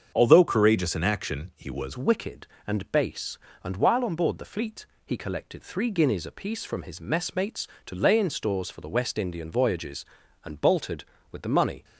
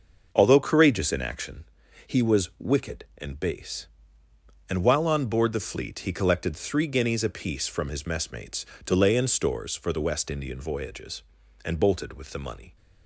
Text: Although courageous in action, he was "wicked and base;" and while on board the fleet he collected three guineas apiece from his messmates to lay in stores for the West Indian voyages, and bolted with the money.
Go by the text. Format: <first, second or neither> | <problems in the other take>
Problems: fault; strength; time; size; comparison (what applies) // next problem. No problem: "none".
second | starts louder than the rest; until 1.1 s; 7 dB; noticeable in the second // changes voice at "wicked"; from 1.9 s on; 9.9 s long // pauses between "fleet" and "he"; slight; at 4.8 s; 0.18 s long